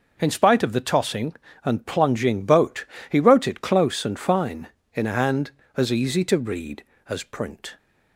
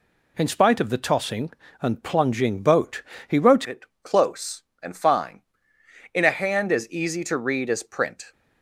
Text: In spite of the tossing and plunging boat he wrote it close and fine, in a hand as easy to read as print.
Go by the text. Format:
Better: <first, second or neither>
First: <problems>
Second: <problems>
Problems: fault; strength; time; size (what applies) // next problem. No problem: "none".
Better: first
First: pauses between "boat" and "he"; slight; at 2.8 s; 0.24 s long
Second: pauses between "boat" and "he"; slight; at 3.0 s; 0.26 s long // changes voice at "it"; from 3.6 s on; 4.7 s long // pauses between "it" and "close"; slight; at 3.8 s; 0.20 s long